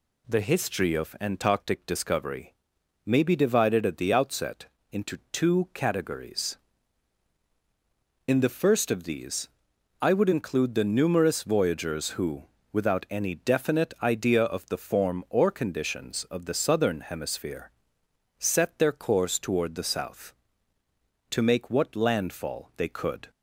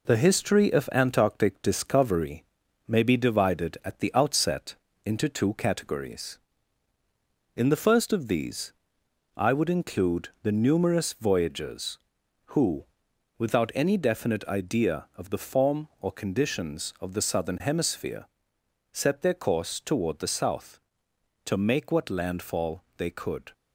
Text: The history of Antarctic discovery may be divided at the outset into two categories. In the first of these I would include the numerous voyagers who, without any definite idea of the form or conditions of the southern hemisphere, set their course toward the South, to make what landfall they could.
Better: first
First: pauses between "discovery" and "may"; noticeable; at 2.5 s; 0.50 s long // pauses between "outset" and "into"; slight; at 4.6 s; 0.26 s long // pauses between "these" and "I"; noticeable; at 9.4 s; 0.52 s long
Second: gets quieter; noticeable; throughout; 4 dB // pauses between "discovery" and "may"; at 2.4 s; 0.42 s long // pauses between "outset" and "into"; slight; at 4.7 s; 0.28 s long // pauses between "these" and "I"; noticeable; at 8.7 s; 0.64 s long // pauses between "include" and "the"; slight; at 10.2 s; 0.16 s long

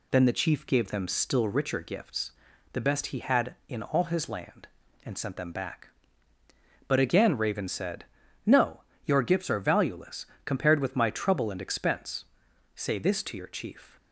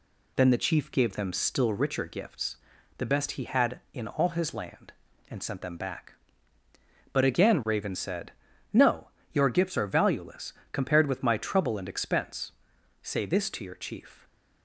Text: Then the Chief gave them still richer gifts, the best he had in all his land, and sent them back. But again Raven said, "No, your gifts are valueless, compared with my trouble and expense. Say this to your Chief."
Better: neither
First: none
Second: none

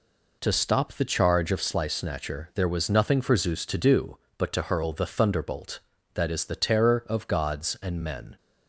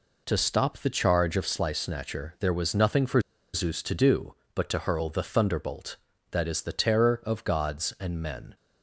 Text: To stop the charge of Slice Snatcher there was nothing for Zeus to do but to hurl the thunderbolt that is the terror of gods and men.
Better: first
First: none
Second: pauses between "for" and "Zeus"; slight; at 3.1 s; 0.34 s long

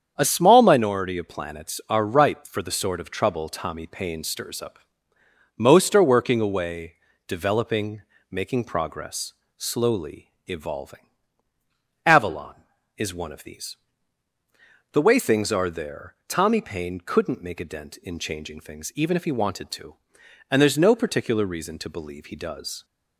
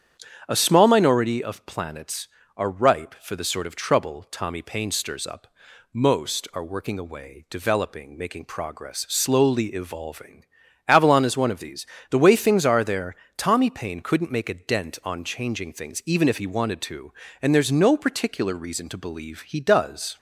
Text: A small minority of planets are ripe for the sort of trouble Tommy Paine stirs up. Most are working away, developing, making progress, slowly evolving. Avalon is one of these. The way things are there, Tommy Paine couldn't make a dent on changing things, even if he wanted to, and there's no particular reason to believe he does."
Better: second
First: starts louder than the rest; strong; until 1.1 s; 7.5 dB // pauses between "slowly" and "evolving"; slight; at 10.3 s; 0.16 s long // says "in" for "on"; at 17.9 s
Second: starts louder than the rest; strong; until 1.4 s; 8 dB

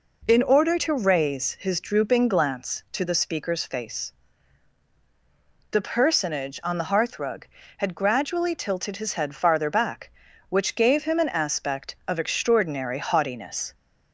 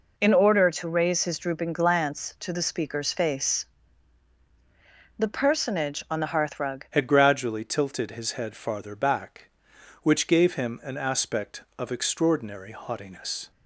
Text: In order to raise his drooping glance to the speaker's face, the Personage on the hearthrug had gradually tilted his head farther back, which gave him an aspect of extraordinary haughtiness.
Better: first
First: none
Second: changes voice at "had"; from 6.9 s on; 6.6 s long

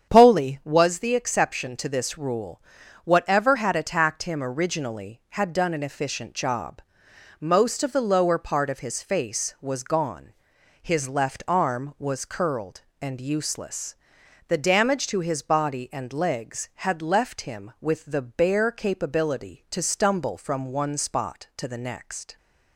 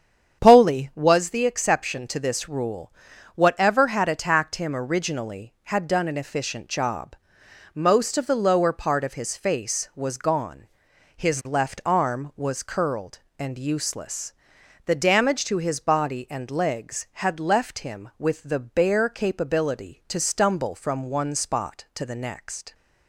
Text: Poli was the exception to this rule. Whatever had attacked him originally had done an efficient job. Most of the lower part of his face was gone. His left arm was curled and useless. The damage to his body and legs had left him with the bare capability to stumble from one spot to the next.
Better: neither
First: starts louder than the rest; strong; until 1.1 s; 8 dB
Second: starts louder than the rest; strong; until 1.4 s; 8 dB

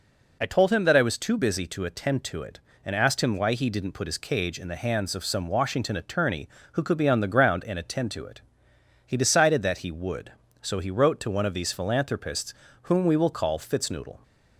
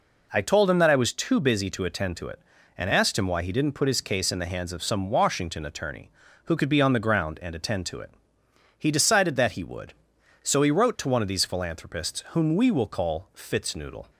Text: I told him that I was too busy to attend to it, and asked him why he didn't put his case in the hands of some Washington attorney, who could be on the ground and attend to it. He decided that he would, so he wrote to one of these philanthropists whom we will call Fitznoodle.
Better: second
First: says "cage" for "case"; at 4.1 s // pauses between "philanthropists" and "whom"; slight; at 12.5 s; 0.28 s long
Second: none

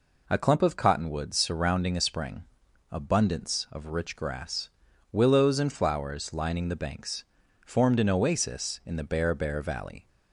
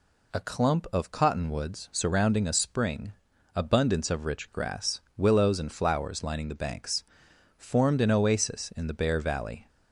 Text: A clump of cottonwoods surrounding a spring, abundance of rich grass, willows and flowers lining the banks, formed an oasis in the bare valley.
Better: second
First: says "bare" twice; at 9.3 s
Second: none

